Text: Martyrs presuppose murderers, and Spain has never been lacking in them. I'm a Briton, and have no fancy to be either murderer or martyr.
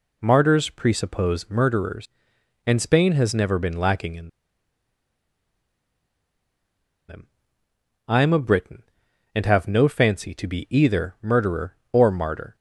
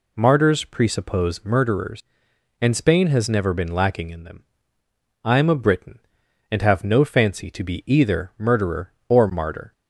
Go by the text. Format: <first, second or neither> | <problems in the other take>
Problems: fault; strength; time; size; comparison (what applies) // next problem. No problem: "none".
second | pauses between "in" and "them"; strong; at 4.2 s; 2.7 s long